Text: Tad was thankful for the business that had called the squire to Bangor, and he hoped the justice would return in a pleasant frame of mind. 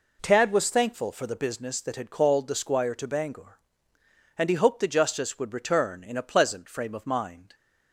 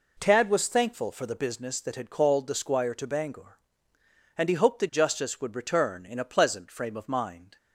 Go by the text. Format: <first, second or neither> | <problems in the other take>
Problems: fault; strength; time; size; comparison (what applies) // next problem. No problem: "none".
neither | none